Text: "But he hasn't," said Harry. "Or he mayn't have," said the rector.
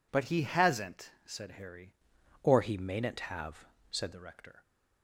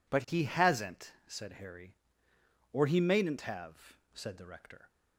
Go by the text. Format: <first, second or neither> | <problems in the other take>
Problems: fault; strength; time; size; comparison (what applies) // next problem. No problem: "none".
second | changes voice from "Or" to "said"; from 2.4 to 4.1 s; 1.7 s long